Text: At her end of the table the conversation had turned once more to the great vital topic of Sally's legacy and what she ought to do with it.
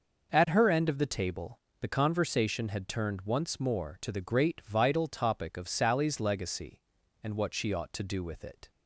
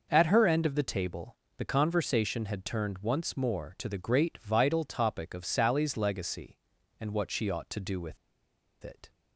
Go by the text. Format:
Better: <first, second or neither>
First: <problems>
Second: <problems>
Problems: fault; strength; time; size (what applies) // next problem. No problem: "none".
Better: first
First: pauses between "table" and "the"; slight; at 1.5 s; 0.22 s long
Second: pauses between "table" and "the"; slight; at 1.3 s; 0.22 s long // pauses between "with" and "it"; noticeable; at 8.1 s; 0.66 s long